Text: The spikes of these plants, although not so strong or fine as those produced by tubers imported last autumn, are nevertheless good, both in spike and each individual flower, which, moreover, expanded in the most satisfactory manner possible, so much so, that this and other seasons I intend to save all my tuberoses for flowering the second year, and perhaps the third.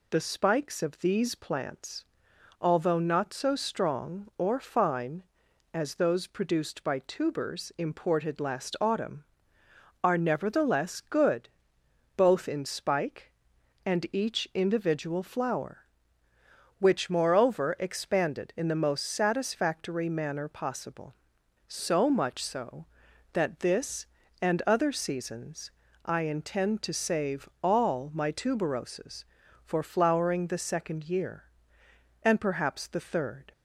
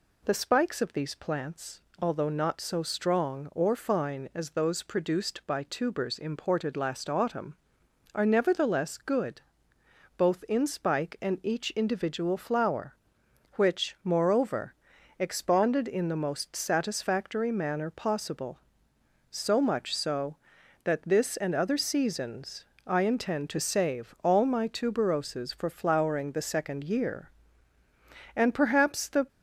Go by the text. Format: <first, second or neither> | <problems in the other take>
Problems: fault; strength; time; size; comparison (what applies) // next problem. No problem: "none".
first | pauses between "seasons" and "I"; slight; at 22.6 s; 0.22 s long; slight in the first // stops before "third"; at 29.2 s